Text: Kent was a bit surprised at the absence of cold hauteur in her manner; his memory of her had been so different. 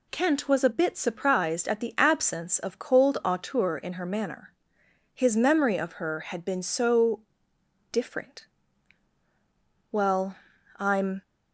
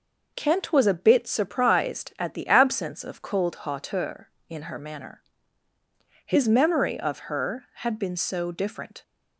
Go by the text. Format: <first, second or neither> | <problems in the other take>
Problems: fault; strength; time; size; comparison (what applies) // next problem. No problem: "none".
second | pauses between "so" and "different"; noticeable; at 7.2 s; 0.68 s long // goes on to say "Well I'm"; noticeable; from 9.9 s on; 1.3 s long